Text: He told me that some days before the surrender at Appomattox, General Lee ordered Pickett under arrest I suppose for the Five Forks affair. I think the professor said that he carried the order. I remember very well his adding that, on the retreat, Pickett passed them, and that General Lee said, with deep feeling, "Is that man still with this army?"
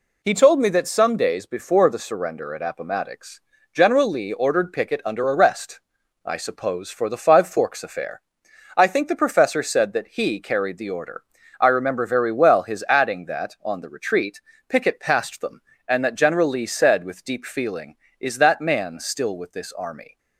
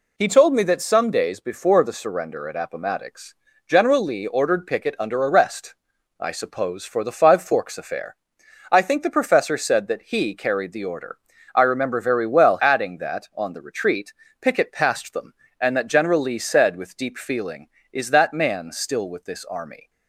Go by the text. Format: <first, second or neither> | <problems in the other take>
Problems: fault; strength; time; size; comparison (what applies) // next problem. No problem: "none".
first | pauses between "arrest" and "I"; noticeable; at 5.7 s; 0.46 s long; noticeable in the first // skips "his"; at 12.6 s